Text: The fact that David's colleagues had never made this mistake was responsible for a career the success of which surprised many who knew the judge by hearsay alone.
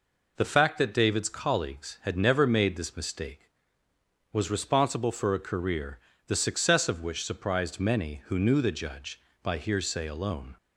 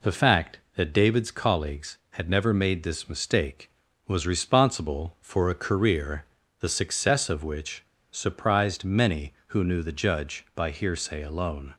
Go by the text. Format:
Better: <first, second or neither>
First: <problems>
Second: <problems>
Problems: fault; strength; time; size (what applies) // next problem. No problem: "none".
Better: first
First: pauses between "career" and "the"; slight; at 5.9 s; 0.27 s long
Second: pauses between "career" and "the"; slight; at 6.2 s; 0.36 s long // pauses between "which" and "surprised"; slight; at 7.8 s; 0.27 s long